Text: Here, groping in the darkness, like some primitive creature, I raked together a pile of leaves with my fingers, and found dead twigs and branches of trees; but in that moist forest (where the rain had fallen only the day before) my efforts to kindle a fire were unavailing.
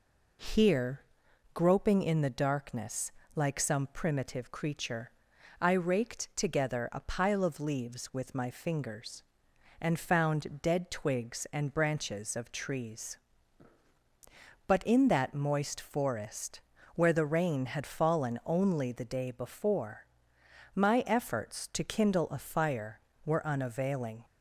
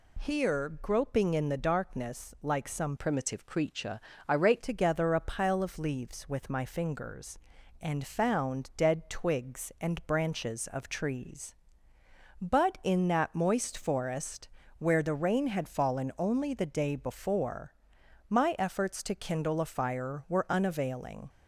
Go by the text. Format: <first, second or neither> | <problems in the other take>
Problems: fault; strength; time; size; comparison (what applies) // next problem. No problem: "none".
first | changes voice from "primitive" to "raked"; from 2.9 to 4.6 s; 1.7 s long